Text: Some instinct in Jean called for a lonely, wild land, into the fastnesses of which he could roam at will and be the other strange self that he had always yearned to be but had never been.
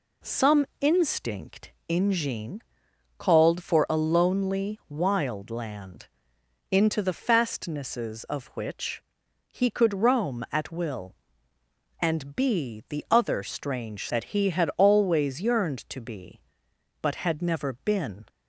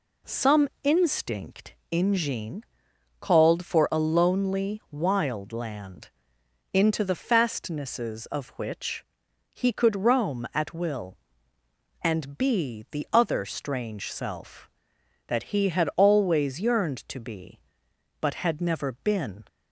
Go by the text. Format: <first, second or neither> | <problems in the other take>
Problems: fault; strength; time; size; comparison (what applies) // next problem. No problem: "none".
second | pauses between "Jean" and "called"; noticeable; at 2.6 s; 0.56 s long; noticeable in the second // pauses between "which" and "he"; noticeable; at 9.0 s; 0.46 s long; noticeable in the second // skips "self"; at 14.0 s